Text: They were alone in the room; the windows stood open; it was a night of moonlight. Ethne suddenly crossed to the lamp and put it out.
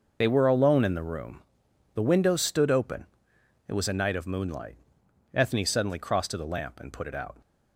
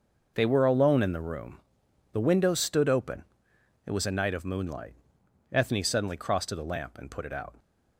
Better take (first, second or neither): second